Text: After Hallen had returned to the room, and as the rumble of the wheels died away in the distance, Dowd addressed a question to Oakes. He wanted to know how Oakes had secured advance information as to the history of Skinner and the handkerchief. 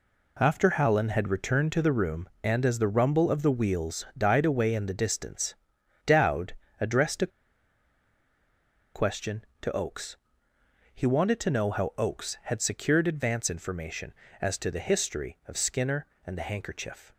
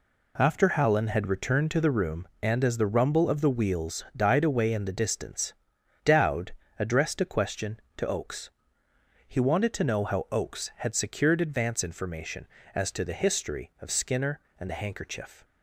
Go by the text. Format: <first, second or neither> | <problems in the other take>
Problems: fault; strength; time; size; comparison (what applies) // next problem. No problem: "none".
second | pauses between "Dowd" and "addressed"; slight; at 6.5 s; 0.26 s long; slight in the second // pauses between "a" and "question"; strong; at 7.3 s; 1.6 s long